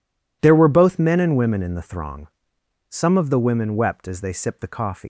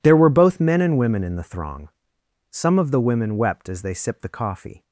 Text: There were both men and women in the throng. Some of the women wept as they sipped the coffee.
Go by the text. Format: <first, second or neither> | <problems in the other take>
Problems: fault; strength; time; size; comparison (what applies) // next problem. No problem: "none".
second | leaves "coffee" unfinished; at 5.0 s; 130 ms